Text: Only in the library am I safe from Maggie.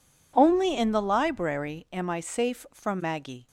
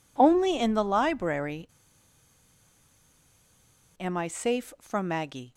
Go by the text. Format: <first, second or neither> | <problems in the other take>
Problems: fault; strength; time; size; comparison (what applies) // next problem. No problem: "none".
first | pauses between "library" and "am"; strong; at 1.6 s; 2.3 s long